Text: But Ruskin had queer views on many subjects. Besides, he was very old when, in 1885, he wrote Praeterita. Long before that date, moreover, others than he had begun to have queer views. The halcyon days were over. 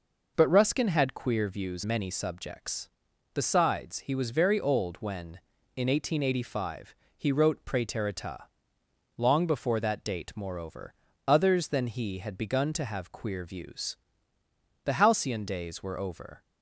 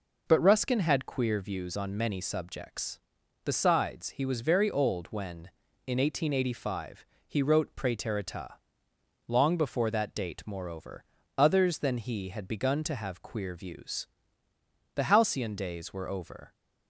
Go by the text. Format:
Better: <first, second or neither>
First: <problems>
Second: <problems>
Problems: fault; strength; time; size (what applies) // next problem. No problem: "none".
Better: second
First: skips "on"; at 1.8 s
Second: none